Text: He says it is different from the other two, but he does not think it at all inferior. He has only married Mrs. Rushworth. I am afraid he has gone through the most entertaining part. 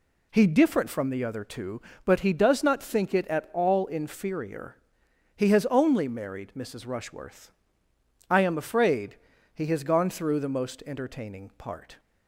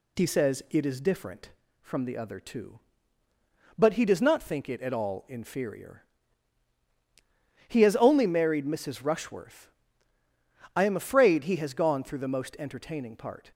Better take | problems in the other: second | skips "says it is"; at 0.4 s // pauses between "afraid" and "he"; at 9.1 s; 0.40 s long

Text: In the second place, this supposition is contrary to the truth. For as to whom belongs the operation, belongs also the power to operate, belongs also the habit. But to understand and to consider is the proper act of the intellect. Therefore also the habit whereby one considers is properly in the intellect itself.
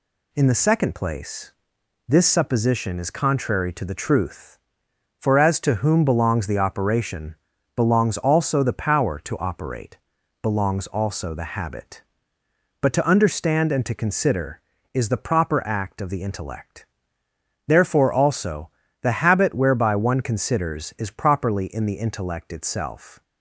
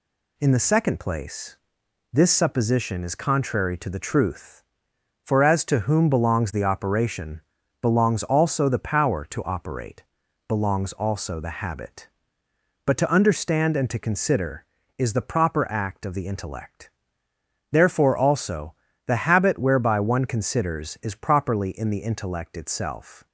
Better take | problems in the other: neither | pauses between "also" and "the"; slight; the same in both

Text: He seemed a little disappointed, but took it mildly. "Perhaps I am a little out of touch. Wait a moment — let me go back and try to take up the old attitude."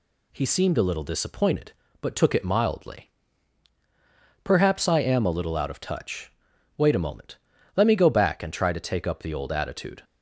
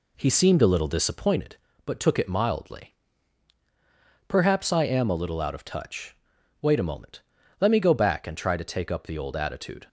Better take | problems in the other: first | starts louder than the rest; slight; until 1.3 s; 2 dB

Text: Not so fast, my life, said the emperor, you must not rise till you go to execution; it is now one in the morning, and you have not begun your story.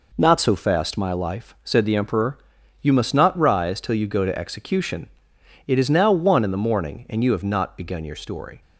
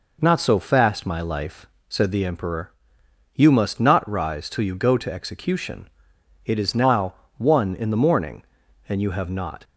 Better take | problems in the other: first | pauses between "now" and "one"; slight; at 7.1 s; 0.24 s long // stops before "begun your story"; at 9.6 s

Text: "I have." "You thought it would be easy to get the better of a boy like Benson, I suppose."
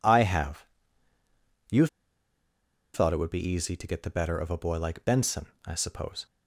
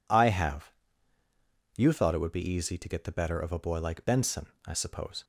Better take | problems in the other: second | pauses between "You" and "thought"; at 1.8 s; 1.0 s long

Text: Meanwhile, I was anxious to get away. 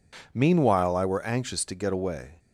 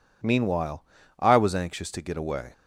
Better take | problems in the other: second | says "were" for "was"; at 1.0 s

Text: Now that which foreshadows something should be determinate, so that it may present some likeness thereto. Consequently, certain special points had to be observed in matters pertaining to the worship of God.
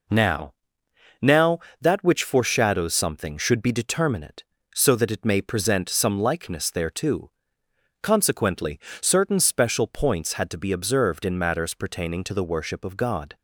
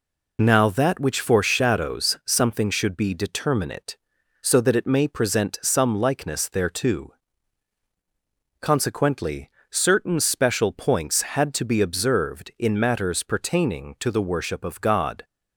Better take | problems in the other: second | says "Now" twice; at 1.1 s

